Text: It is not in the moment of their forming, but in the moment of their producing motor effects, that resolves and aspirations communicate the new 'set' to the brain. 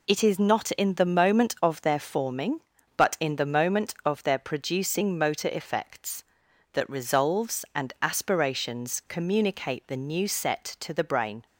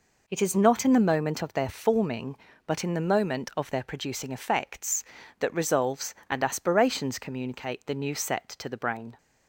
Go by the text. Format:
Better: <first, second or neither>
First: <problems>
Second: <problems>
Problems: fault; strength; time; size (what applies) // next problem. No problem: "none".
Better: first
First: none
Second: skips "motor"; at 4.3 s